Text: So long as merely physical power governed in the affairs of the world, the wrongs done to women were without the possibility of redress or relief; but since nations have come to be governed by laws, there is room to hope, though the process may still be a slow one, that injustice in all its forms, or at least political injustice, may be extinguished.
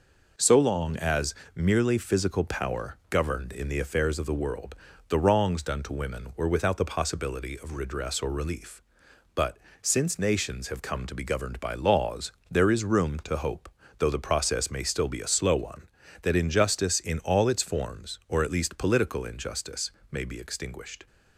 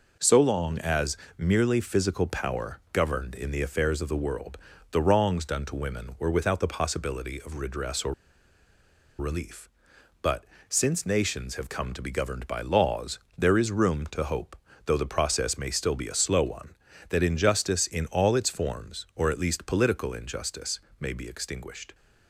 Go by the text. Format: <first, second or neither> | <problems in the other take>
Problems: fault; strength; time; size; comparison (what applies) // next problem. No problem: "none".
first | pauses between "as" and "merely"; slight; at 1.1 s; 0.22 s long; slight in the first // pauses between "or" and "relief"; at 8.1 s; 1.0 s long // pauses between "but" and "since"; slight; at 10.4 s; 0.24 s long; slight in the first